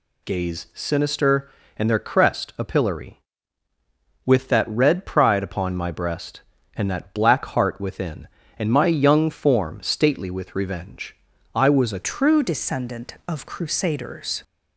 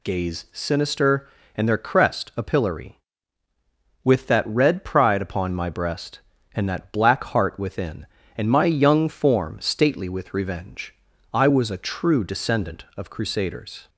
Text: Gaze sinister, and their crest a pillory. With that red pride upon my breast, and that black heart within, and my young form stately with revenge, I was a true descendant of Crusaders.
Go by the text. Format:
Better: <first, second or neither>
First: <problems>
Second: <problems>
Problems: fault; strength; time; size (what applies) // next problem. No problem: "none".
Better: second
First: changes voice at "true"; from 11.9 s on; 2.5 s long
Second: none